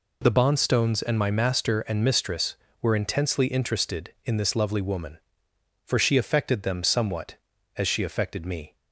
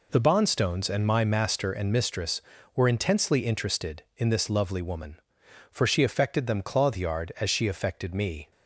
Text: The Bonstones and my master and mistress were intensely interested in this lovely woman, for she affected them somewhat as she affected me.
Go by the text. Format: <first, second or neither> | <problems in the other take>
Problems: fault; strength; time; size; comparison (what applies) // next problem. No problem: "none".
first | says "clothyard" for "somewhat"; at 6.6 s